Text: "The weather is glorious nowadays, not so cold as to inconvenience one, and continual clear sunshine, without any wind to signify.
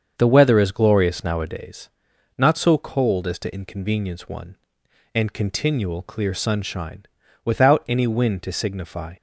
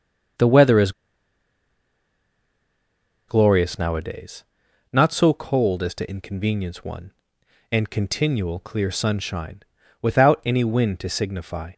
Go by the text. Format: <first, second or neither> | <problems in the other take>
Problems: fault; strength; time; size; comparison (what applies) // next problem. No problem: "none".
first | starts louder than the rest; until 3.7 s; 7 dB; also in the first // pauses between "is" and "glorious"; strong; at 0.9 s; 2.3 s long